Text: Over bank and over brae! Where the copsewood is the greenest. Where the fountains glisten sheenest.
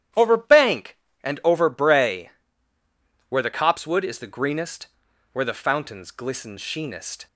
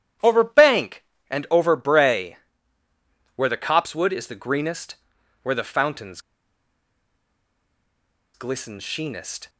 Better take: first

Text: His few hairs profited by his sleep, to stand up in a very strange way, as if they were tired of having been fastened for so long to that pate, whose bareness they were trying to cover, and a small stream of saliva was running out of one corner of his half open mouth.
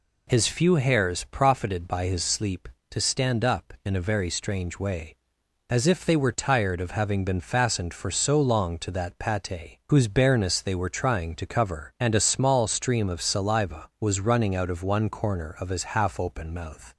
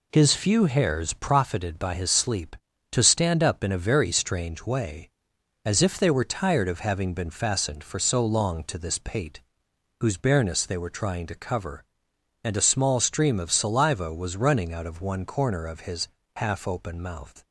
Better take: first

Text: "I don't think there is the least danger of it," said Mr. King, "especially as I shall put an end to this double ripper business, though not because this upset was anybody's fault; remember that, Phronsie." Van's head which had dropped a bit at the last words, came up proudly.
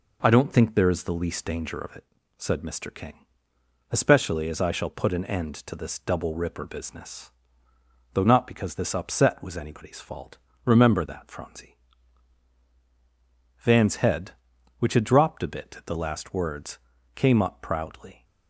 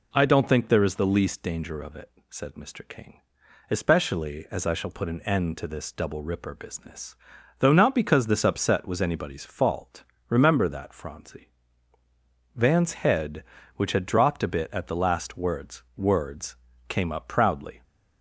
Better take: first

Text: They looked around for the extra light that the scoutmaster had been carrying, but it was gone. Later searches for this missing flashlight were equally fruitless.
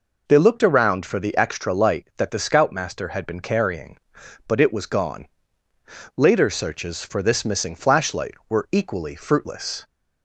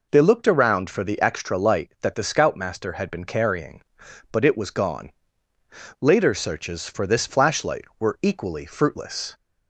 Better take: first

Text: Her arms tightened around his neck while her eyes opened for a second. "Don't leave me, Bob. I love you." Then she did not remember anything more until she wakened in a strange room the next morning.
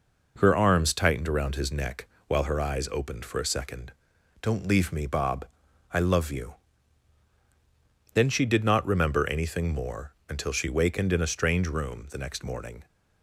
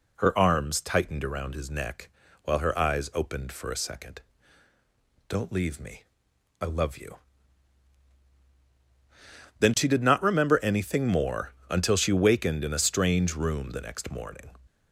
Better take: first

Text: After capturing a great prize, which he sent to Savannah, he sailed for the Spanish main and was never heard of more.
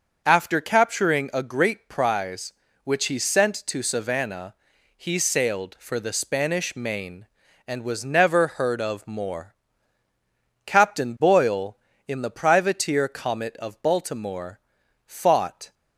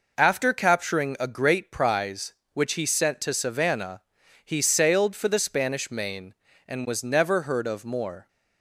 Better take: second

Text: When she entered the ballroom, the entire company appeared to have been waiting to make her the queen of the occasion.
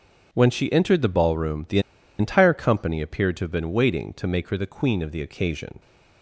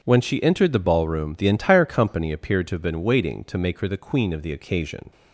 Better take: second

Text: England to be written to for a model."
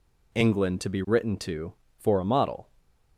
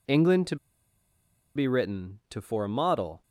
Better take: first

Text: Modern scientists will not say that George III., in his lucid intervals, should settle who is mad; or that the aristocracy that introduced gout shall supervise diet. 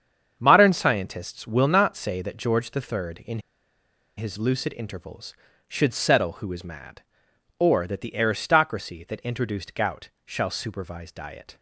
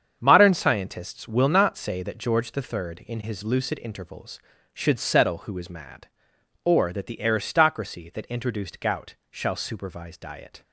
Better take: second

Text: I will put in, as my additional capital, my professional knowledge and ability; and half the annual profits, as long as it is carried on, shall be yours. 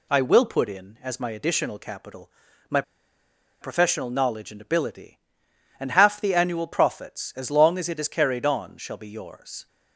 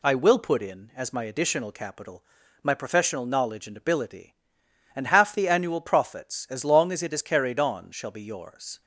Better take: second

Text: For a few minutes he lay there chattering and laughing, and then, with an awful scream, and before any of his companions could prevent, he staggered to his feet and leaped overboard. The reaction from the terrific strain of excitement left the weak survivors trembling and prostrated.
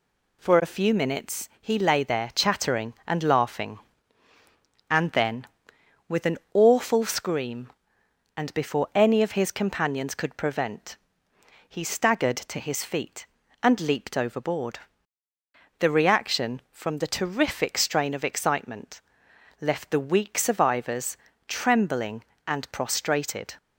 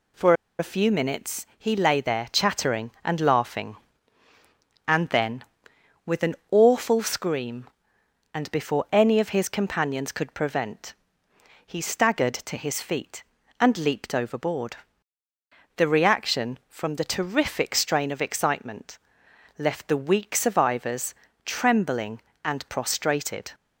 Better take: first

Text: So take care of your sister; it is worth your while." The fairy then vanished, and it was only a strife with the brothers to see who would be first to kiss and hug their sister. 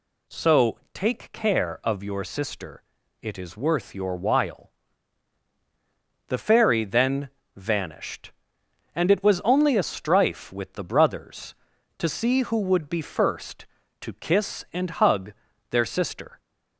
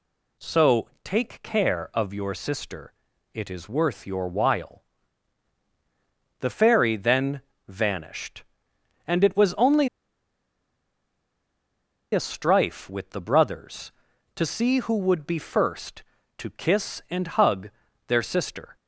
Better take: first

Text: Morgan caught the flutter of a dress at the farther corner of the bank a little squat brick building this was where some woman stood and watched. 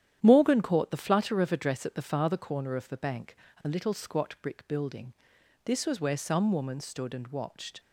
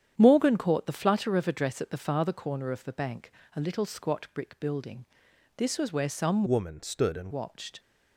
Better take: first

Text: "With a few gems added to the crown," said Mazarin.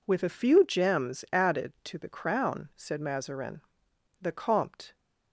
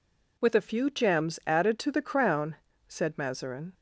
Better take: second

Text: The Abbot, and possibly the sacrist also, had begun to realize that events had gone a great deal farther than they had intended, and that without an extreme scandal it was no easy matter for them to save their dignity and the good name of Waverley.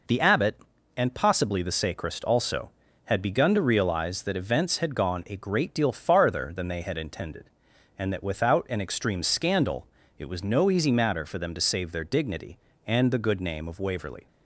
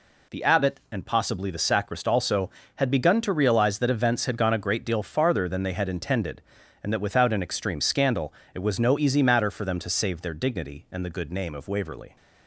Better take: neither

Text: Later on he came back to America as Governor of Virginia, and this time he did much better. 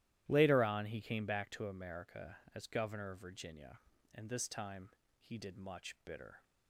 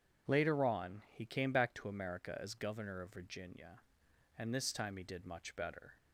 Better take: second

